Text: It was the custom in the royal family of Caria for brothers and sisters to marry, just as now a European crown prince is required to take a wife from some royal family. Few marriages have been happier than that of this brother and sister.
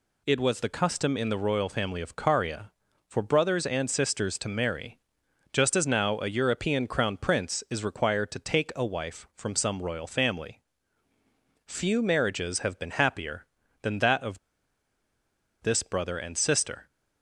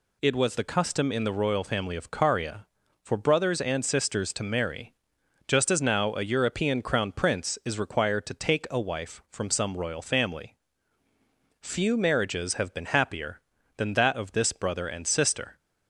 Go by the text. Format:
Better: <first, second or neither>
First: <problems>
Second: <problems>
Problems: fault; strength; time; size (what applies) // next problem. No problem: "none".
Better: second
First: pauses between "of" and "this"; at 14.3 s; 1.2 s long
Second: none